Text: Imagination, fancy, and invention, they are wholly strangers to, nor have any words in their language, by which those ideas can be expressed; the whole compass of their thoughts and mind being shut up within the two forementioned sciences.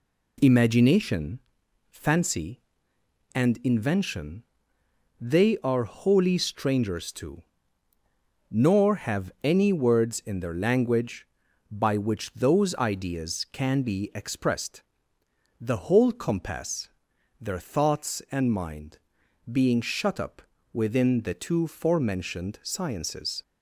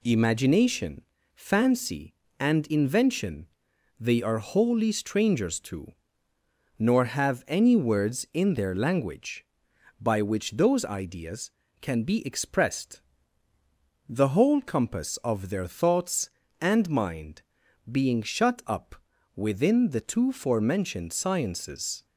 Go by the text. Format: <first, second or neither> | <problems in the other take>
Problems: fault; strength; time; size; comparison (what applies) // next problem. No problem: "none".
second | skips "of"; at 17.1 s // pauses between "mind" and "being"; noticeable; at 18.9 s; 0.52 s long; also in the second // pauses between "up" and "within"; slight; at 20.4 s; 0.30 s long; also in the second